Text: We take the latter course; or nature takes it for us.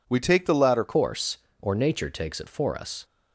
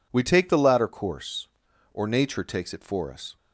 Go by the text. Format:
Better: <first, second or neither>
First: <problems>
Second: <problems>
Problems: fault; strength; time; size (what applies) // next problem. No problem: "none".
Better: second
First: changes voice at "course"; from 0.8 s on; 2.2 s long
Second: none